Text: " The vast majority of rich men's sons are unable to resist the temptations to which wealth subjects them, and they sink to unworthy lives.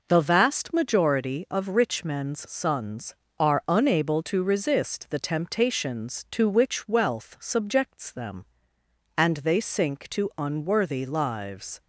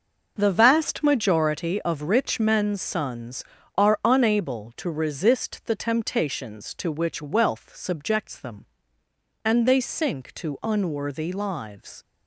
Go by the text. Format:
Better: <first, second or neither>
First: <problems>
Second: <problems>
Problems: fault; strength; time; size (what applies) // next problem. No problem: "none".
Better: neither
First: none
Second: none